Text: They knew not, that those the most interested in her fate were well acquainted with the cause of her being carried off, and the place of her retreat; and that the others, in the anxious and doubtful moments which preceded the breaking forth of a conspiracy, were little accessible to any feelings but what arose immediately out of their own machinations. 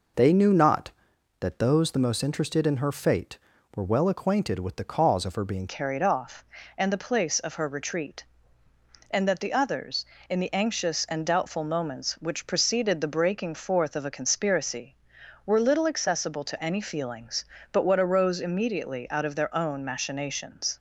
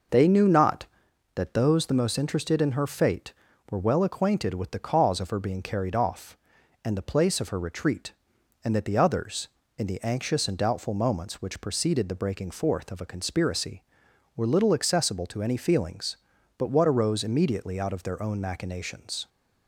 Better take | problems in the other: second | changes voice at "carried"; from 5.6 s on; 15.1 s long

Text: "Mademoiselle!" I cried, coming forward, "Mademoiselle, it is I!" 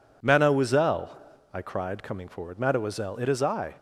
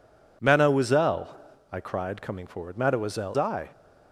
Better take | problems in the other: first | skips "it is"; at 3.3 s

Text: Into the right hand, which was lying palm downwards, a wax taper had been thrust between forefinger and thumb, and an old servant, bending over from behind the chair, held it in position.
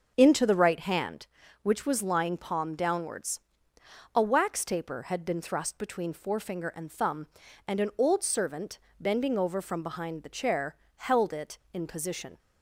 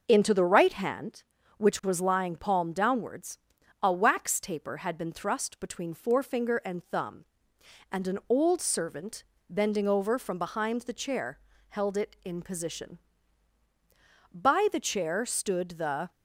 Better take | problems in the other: first | starts louder than the rest; until 1.0 s; 6 dB; also in the first // goes on to say "By the chair stood the"; strong; from 14.3 s on; 1.7 s long

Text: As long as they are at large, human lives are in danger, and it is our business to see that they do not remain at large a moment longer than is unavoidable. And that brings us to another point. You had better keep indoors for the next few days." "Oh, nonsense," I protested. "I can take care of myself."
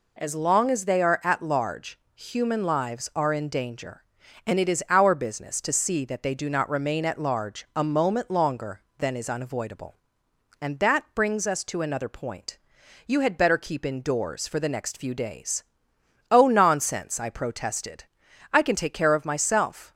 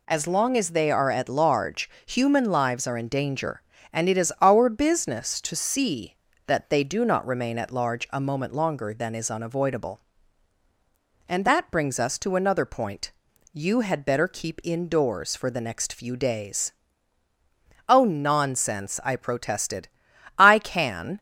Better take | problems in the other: first | stops before "take care of myself"; at 21.1 s

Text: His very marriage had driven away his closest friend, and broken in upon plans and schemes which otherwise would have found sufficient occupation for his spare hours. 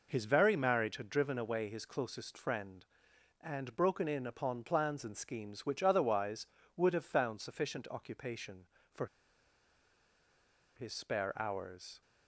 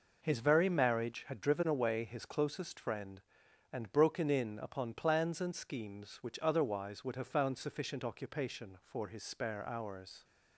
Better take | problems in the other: second | pauses between "for" and "his"; strong; at 9.0 s; 1.7 s long

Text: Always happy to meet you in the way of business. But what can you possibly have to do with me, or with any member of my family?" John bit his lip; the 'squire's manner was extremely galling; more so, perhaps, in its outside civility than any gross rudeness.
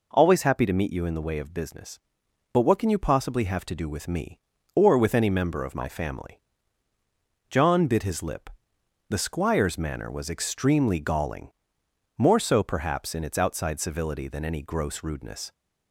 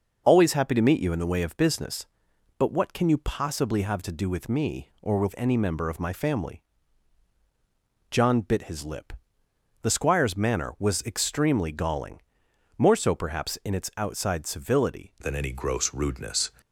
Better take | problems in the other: first | changes voice at "than"; from 15.2 s on; 1.3 s long

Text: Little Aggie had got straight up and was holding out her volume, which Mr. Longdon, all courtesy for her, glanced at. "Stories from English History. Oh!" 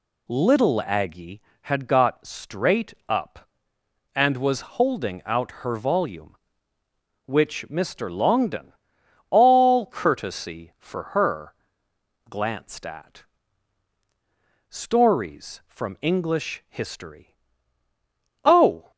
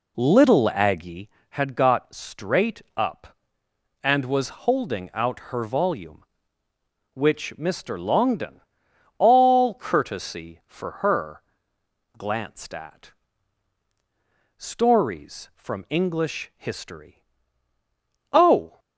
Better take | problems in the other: first | starts louder than the rest; slight; until 1.4 s; 2.5 dB

